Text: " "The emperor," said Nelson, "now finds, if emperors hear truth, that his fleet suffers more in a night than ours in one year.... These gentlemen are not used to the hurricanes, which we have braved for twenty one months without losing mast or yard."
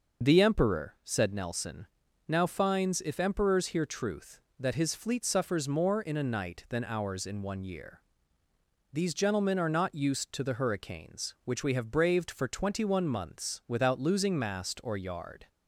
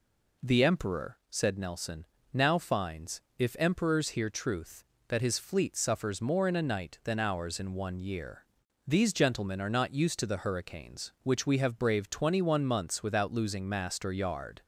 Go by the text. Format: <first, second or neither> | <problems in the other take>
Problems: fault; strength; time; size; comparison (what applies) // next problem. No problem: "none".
first | skips "for"; at 12.1 s